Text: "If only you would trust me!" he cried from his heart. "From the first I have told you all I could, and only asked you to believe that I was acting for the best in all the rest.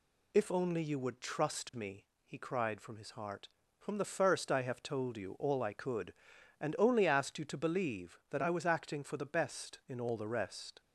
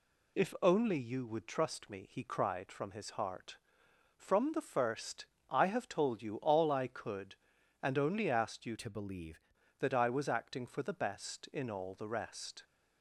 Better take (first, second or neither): first